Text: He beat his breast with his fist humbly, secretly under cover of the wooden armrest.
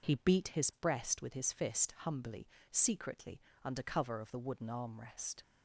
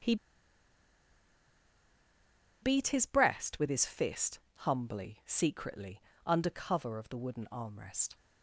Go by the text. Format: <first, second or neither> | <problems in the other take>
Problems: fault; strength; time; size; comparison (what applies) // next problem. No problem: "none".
first | starts louder than the rest; strong; until 3.5 s; 7.5 dB // pauses between "He" and "beat"; strong; at 0.1 s; 2.4 s long // pauses between "fist" and "humbly"; slight; at 4.3 s; 0.20 s long // pauses between "secretly" and "under"; slight; at 5.9 s; 0.26 s long; slight in the first